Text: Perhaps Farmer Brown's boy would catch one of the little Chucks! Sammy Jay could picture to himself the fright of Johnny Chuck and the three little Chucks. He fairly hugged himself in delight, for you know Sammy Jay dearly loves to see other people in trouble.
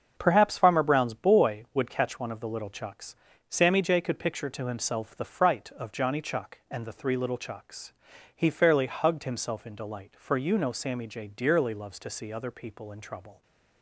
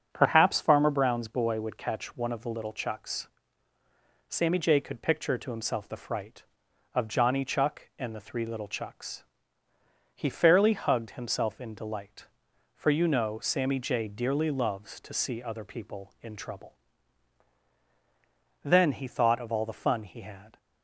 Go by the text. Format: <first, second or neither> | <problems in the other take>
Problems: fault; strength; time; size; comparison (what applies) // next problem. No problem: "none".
first | starts louder than the rest; until 1.1 s; 7 dB; also in the first // goes on to say "Then he thought of all the fun he had"; strong; from 18.6 s on; 1.9 s long